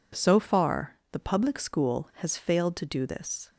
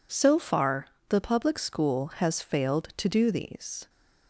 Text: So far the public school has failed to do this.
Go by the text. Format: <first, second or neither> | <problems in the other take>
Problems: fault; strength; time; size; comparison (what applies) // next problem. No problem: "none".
first | pauses between "far" and "the"; slight; at 0.8 s; 0.22 s long // says "these" for "this"; at 3.2 s